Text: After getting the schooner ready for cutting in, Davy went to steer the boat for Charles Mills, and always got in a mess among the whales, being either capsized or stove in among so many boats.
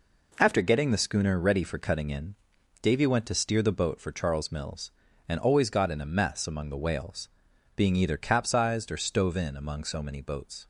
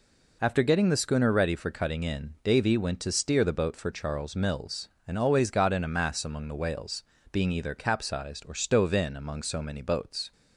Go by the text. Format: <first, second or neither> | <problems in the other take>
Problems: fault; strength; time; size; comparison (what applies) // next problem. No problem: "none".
first | says "mass" for "mess"; at 5.8 s